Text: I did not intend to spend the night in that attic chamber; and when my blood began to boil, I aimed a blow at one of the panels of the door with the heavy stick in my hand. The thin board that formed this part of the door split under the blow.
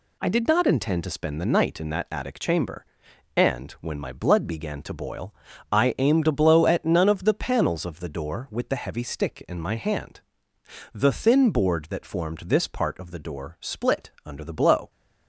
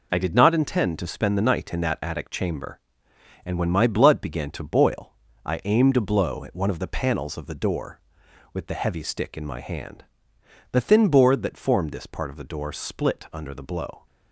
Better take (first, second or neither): second